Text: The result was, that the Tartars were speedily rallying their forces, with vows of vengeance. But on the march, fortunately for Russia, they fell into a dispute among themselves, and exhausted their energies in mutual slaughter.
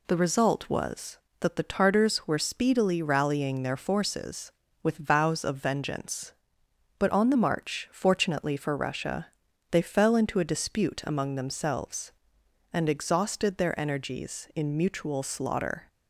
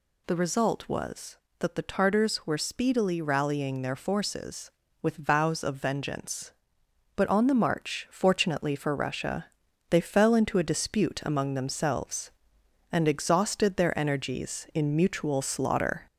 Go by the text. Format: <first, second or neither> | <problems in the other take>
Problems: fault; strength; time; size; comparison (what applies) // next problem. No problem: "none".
first | gets louder; slight; throughout; 3 dB